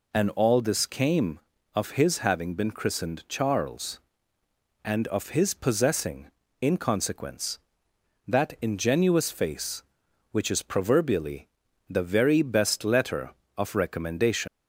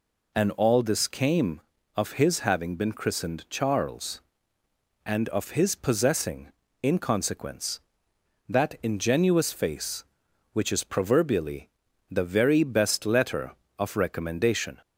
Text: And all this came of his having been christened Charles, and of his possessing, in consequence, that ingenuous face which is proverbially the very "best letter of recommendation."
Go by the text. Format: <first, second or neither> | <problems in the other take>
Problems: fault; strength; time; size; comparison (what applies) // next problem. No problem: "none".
second | pauses between "proverbially" and "the"; at 11.4 s; 0.42 s long; also in the second // leaves "recommendation" unfinished; at 14.4 s; 115 ms